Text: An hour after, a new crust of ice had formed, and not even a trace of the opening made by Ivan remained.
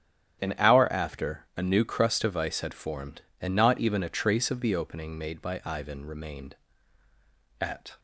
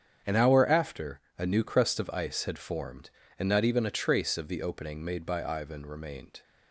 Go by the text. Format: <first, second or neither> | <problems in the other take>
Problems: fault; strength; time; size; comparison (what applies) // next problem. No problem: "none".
second | starts louder than the rest; strong; until 1.4 s; 10 dB; strong in the second // goes on to say "At"; slight; from 7.5 s on; 0.40 s long